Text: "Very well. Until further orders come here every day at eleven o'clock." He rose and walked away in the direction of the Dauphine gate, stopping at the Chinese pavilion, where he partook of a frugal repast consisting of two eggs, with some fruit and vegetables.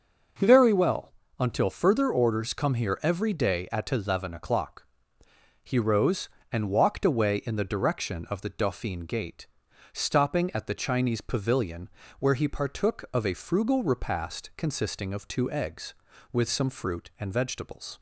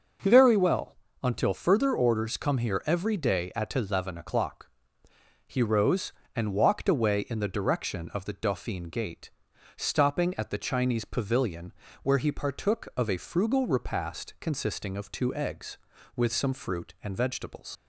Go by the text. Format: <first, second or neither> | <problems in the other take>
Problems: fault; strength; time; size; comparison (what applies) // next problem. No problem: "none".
first | starts louder than the rest; noticeable; until 1.4 s; 6 dB; also in the first // leaves "vegetables" unfinished; at 17.7 s; 75 ms